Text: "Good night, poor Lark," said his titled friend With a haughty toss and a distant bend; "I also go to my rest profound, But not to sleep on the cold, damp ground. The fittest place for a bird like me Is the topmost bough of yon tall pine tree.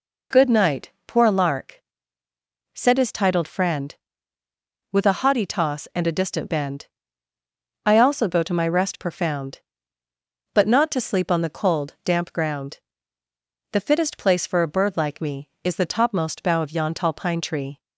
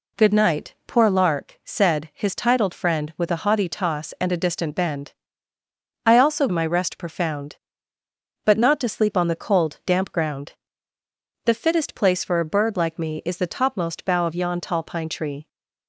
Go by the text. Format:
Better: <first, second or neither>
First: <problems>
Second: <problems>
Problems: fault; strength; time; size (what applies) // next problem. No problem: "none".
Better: first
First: none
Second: skips "go to"; at 6.4 s